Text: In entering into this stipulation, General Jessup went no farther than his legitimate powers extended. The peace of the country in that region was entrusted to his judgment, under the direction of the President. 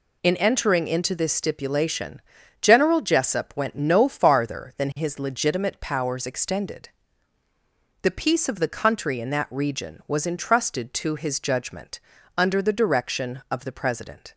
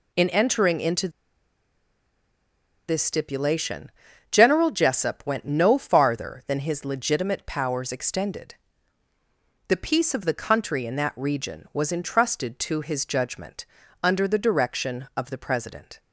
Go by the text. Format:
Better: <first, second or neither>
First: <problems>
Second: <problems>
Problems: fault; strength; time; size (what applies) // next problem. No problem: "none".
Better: first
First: none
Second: pauses between "into" and "this"; strong; at 1.0 s; 1.7 s long